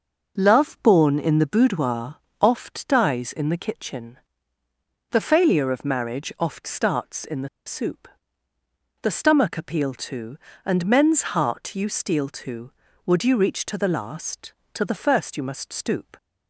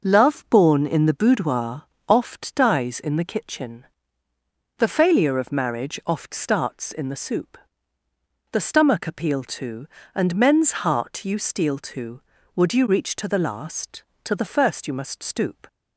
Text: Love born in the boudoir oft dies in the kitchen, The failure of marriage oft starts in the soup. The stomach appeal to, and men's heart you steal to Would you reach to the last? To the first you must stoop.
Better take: second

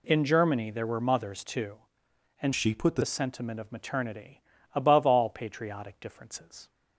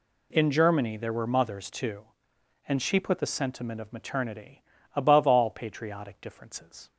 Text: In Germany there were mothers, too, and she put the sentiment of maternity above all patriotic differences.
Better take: second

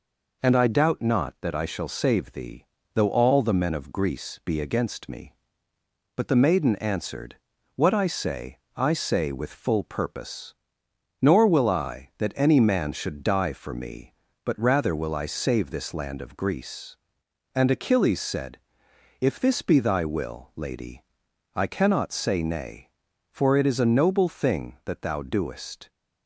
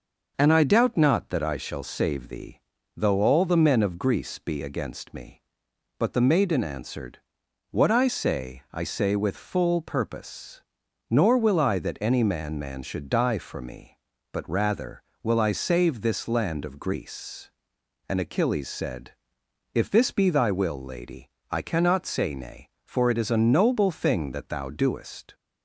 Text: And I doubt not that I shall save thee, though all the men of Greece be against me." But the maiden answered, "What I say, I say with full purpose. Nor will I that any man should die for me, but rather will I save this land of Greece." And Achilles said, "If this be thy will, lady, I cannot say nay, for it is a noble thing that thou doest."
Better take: first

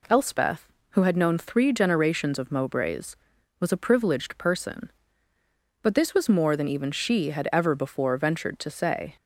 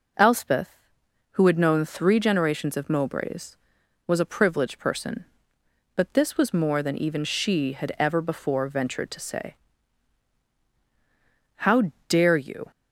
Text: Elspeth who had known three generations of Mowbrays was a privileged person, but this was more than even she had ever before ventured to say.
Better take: first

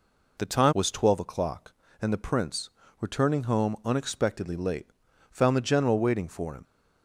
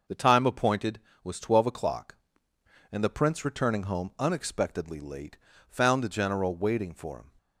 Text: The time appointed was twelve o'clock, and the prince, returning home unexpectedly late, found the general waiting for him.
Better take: second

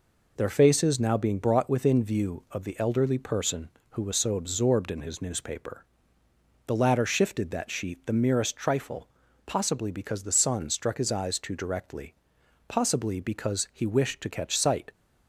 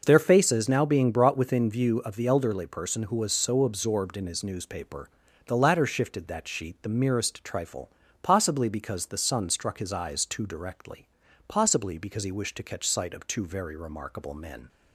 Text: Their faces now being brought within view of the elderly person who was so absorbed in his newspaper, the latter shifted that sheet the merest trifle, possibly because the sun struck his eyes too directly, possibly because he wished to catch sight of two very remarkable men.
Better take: second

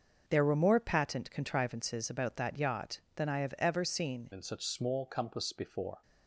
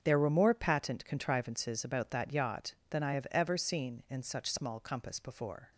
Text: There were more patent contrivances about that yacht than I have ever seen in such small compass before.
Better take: second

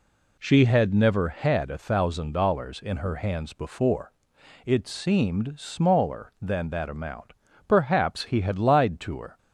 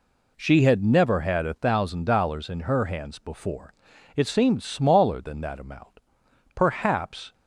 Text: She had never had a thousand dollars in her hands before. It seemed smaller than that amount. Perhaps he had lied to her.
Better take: first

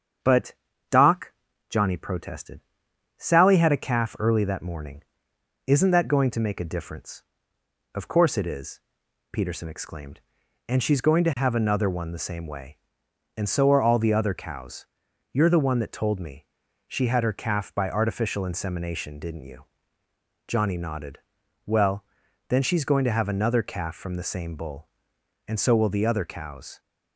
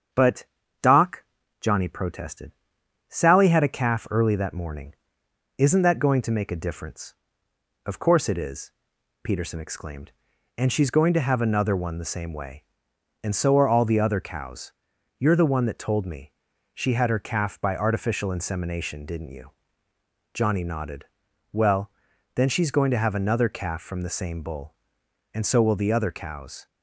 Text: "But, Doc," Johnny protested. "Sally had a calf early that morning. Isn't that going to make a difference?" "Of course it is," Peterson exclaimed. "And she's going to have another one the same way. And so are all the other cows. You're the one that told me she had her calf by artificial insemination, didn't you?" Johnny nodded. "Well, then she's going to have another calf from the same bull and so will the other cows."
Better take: neither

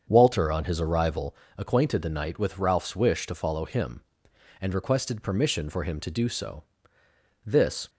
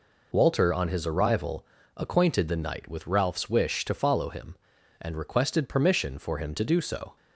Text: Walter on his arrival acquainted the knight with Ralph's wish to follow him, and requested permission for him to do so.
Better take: second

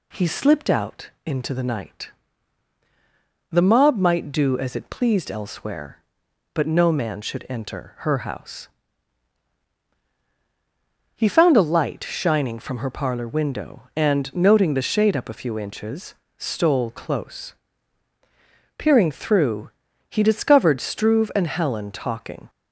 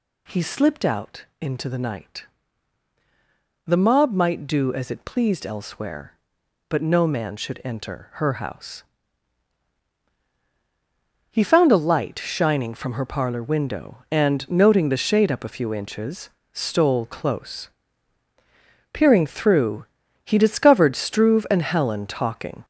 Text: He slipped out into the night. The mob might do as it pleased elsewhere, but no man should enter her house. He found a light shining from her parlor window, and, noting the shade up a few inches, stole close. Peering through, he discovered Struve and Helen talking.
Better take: first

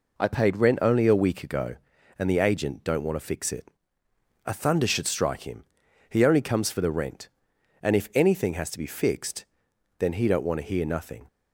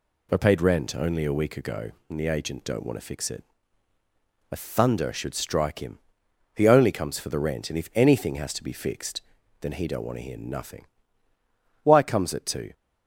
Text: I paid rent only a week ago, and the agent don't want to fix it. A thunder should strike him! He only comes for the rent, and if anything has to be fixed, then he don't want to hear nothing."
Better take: first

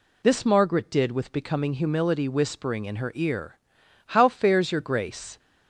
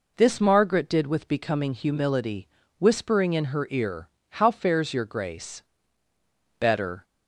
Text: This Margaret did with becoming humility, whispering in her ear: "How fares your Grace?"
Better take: first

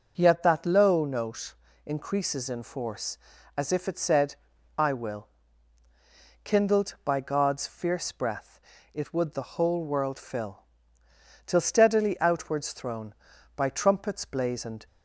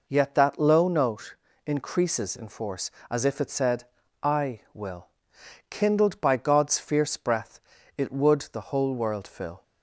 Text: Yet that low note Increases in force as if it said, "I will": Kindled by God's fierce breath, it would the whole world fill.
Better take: second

